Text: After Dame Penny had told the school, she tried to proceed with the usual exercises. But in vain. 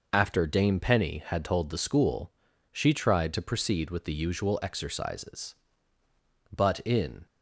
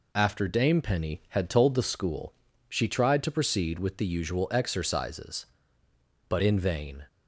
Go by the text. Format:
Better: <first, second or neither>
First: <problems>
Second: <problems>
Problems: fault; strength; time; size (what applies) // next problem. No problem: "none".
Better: second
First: stops before "vain"; at 7.2 s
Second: none